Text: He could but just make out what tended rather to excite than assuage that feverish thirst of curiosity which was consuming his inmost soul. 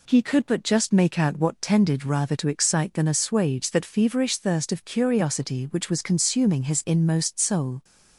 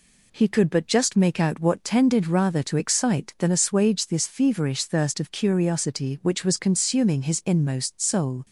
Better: first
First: none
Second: says "this" for "that"; at 4.0 s

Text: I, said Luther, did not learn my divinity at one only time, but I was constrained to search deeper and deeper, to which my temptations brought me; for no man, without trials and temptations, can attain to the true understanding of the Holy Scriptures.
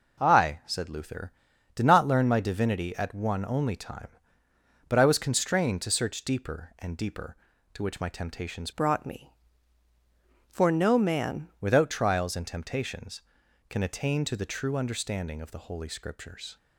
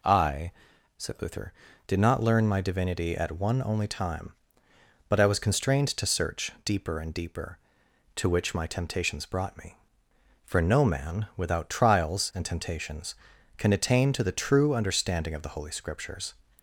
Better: second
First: changes voice from "brought" to "man"; from 8.7 to 11.4 s; 2.7 s long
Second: none

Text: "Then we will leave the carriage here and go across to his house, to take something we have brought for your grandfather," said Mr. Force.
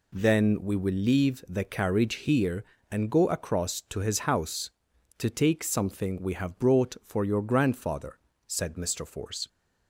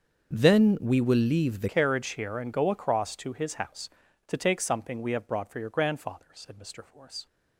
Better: first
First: none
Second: starts louder than the rest; until 1.3 s; 6.5 dB // changes voice at "carriage"; from 1.6 s on; 5.6 s long

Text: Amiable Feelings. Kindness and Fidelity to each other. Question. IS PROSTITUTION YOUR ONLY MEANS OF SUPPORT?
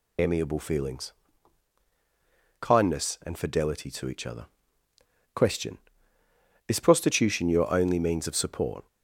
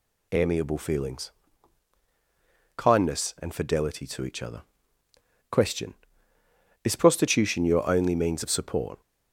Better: second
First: loses the start of "Amiable"; at 0.1 s; 70 ms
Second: none

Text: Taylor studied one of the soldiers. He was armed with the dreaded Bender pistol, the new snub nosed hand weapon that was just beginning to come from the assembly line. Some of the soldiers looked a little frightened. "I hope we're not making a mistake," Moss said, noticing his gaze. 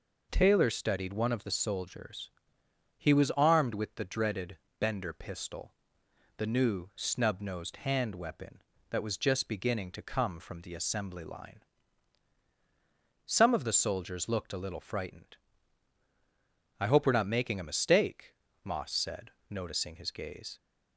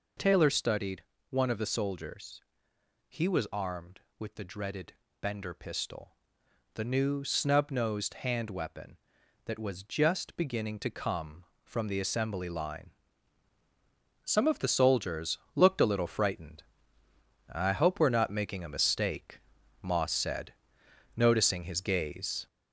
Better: first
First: pauses between "dreaded" and "Bender"; slight; at 4.5 s; 0.22 s long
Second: gets louder; noticeable; throughout; 4.5 dB // pauses between "studied" and "one"; slight; at 1.0 s; 0.26 s long // pauses between "dreaded" and "Bender"; slight; at 4.9 s; 0.26 s long // pauses between "soldiers" and "looked"; slight; at 15.3 s; 0.18 s long

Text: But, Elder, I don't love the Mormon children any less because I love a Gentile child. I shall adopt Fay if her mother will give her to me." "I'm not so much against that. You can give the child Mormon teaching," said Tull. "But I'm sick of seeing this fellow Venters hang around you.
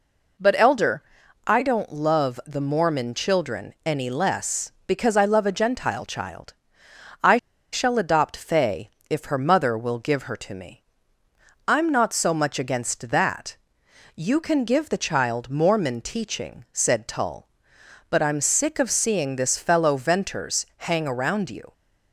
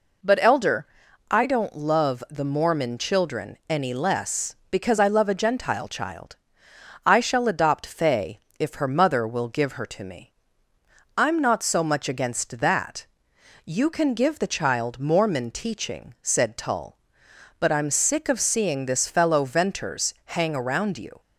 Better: second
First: pauses between "I" and "shall"; slight; at 7.3 s; 0.35 s long // pauses between "Fay" and "if"; slight; at 8.9 s; 0.18 s long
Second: pauses between "Fay" and "if"; slight; at 8.3 s; 0.18 s long

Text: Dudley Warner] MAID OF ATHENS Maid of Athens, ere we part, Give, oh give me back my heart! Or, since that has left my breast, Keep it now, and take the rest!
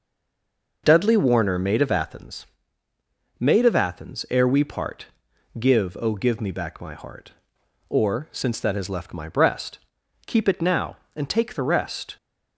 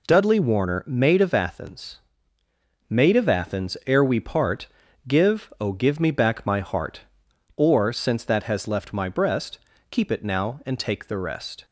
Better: second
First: stays silent before the first word; slight; until 0.8 s; 0.8 s long // pauses between "ATHENS" and "Maid"; noticeable; at 2.4 s; 0.96 s long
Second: pauses between "ATHENS" and "Maid"; noticeable; at 1.9 s; 0.94 s long

